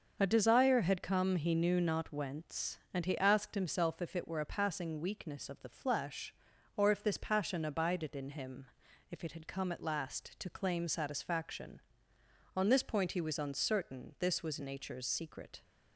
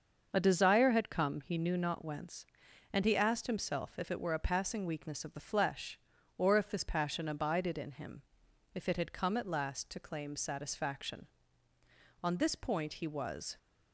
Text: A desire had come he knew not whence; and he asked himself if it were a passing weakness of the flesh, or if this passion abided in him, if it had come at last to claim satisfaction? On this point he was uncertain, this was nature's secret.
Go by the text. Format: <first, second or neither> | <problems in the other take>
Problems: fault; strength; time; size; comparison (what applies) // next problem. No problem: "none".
first | starts louder than the rest; until 1.3 s; 6.5 dB; also in the first // stops before "uncertain this was nature's secret"; at 13.5 s